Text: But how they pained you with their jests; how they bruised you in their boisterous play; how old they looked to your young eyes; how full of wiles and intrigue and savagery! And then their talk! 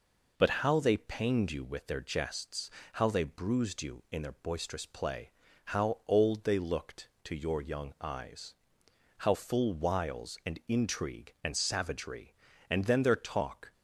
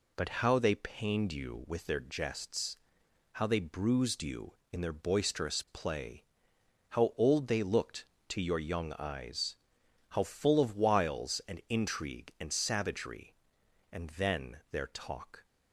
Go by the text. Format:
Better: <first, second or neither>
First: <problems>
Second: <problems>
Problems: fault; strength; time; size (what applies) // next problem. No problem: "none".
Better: second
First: skips "of"; at 9.7 s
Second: none